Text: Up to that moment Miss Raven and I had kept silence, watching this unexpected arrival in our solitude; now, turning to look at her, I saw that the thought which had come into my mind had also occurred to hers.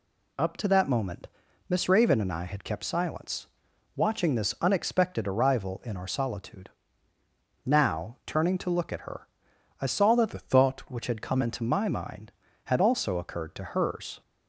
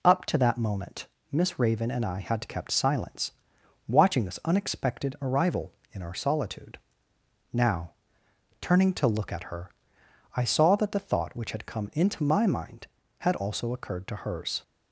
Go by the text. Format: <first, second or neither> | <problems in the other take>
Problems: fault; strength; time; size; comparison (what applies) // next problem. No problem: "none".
second | pauses between "moment" and "Miss"; at 1.2 s; 0.42 s long; slight in the second // changes voice from "the" to "thought"; from 10.3 to 10.8 s; 0.5 s long